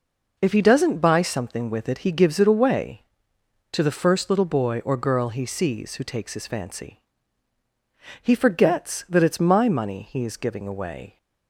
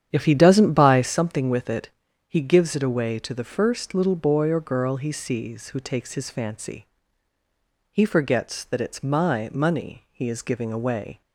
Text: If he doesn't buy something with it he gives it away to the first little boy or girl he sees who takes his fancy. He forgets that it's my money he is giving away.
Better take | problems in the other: first | starts louder than the rest; strong; until 1.2 s; 9 dB // pauses between "it" and "he"; at 1.8 s; 0.38 s long

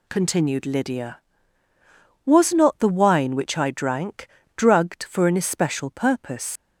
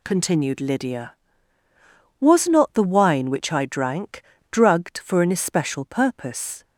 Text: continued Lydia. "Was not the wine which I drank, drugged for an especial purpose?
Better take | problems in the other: second | leaves "purpose" unfinished; at 6.5 s; 135 ms

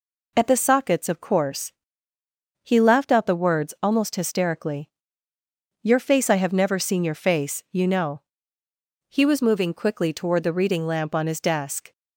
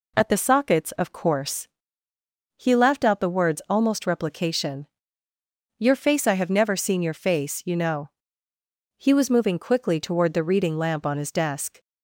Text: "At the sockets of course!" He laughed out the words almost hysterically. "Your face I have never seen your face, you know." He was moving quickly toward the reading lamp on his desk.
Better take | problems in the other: first | says "replication" for "hysterically"; at 4.0 s

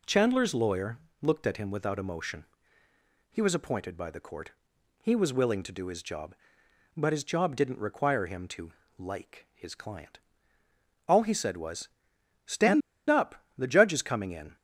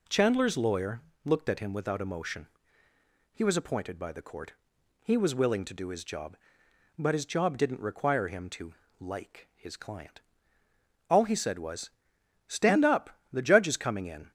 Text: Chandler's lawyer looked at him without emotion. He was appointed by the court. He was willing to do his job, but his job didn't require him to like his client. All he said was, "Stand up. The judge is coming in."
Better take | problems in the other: second | pauses between "lawyer" and "looked"; slight; at 0.9 s; 0.24 s long; slight in the second // pauses between "to" and "like"; slight; at 8.7 s; 0.28 s long; slight in the second // pauses between "Stand" and "up"; slight; at 12.8 s; 0.29 s long

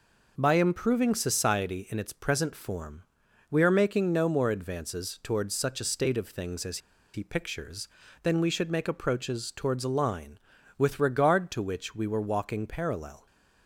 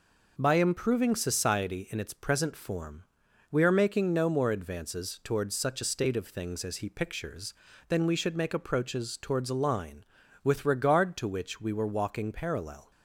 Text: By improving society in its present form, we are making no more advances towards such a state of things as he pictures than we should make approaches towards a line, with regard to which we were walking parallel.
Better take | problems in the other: second | pauses between "as" and "he"; slight; at 6.7 s; 0.35 s long

